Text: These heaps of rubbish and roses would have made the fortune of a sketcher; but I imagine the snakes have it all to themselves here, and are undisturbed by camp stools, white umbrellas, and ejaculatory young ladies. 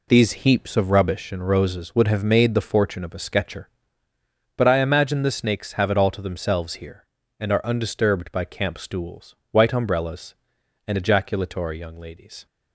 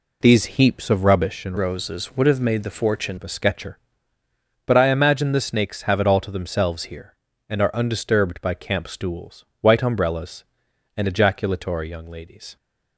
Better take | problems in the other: first | changes voice from "roses" to "fortune"; from 1.5 to 3.1 s; 1.6 s long

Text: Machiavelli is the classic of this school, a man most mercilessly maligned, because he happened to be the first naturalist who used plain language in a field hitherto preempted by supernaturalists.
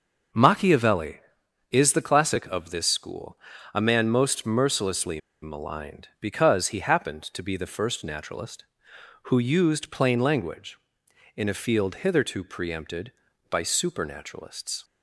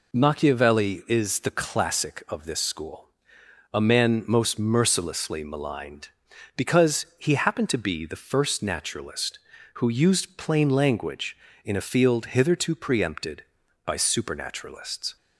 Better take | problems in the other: second | starts louder than the rest; until 1.8 s; 6.5 dB // pauses between "mercilessly" and "maligned"; slight; at 5.1 s; 0.22 s long

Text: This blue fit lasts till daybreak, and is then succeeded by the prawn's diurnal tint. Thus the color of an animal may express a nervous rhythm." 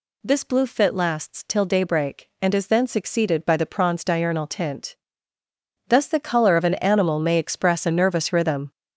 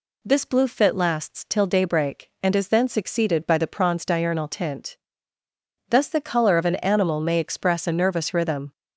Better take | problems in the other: second | gets louder; strong; throughout; 7.5 dB

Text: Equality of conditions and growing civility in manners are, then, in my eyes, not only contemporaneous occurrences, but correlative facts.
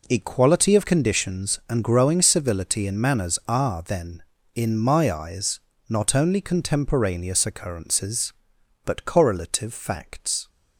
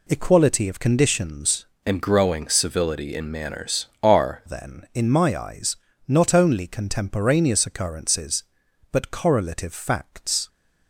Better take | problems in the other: first | changes voice from "and" to "are"; from 1.8 to 4.4 s; 2.6 s long

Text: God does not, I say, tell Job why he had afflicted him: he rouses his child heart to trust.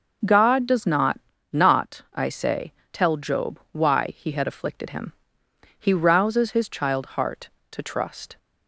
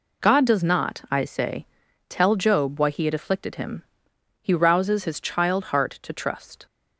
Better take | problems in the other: second | says "not" twice; at 1.5 s

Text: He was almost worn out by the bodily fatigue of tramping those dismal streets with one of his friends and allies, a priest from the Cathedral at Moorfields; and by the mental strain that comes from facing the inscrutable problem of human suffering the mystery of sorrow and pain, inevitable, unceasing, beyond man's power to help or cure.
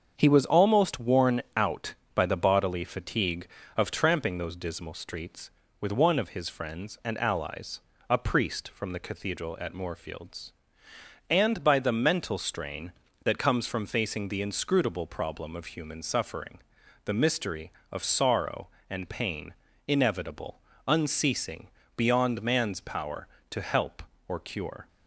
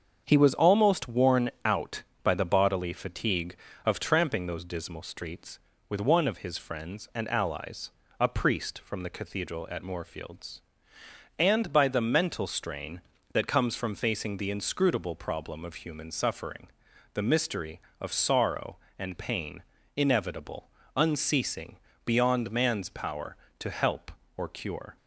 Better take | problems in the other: neither | starts louder than the rest; the same in both // pauses between "suffering" and "the"; the same in both

